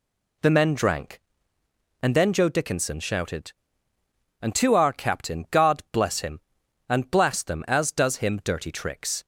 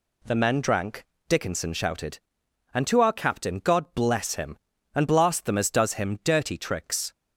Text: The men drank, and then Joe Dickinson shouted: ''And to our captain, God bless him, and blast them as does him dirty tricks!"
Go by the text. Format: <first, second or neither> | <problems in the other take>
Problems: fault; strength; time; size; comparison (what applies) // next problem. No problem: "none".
first | skips "and then Joe"; at 1.1 s